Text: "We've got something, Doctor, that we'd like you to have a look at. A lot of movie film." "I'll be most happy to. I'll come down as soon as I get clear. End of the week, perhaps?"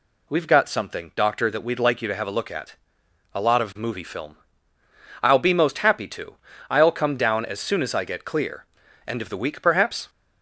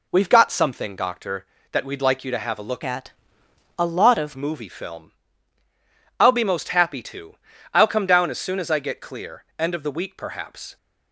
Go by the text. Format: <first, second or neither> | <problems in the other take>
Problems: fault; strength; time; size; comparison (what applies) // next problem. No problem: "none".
first | changes voice from "at" to "of"; from 2.8 to 4.3 s; 1.5 s long